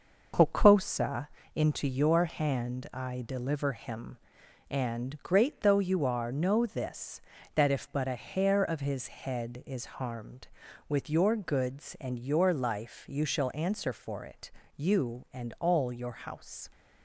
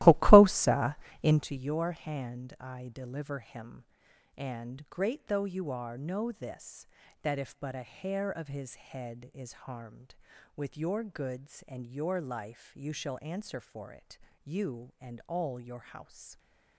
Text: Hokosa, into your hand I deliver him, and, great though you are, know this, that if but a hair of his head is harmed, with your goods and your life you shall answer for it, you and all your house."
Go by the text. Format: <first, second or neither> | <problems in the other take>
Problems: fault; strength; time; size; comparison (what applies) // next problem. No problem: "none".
first | starts louder than the rest; strong; until 1.5 s; 16.5 dB